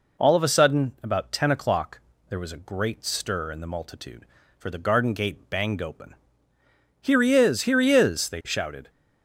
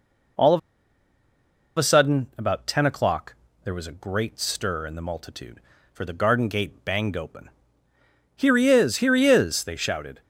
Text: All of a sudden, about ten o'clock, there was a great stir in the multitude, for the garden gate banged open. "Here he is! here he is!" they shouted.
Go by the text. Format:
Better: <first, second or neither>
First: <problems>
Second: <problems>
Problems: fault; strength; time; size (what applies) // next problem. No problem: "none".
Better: first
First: none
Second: pauses between "of" and "a"; at 0.5 s; 1.1 s long